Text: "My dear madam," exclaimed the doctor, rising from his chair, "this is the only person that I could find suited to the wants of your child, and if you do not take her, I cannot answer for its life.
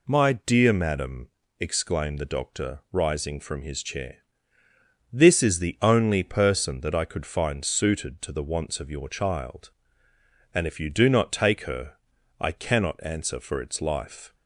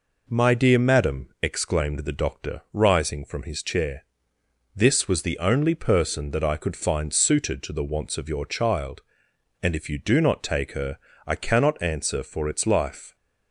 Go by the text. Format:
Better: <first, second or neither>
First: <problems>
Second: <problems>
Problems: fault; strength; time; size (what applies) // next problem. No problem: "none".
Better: first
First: none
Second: says "was" for "is"; at 5.0 s